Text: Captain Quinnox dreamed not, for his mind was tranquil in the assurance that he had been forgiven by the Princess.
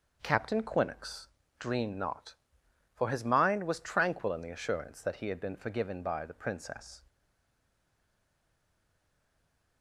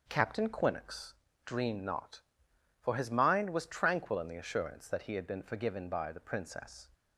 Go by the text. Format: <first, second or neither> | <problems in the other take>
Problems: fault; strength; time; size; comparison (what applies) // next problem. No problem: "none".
second | pauses between "Quinnox" and "dreamed"; slight; at 1.2 s; 0.30 s long; slight in the second // stays silent after the last word; strong; from 7.0 s on; 2.8 s long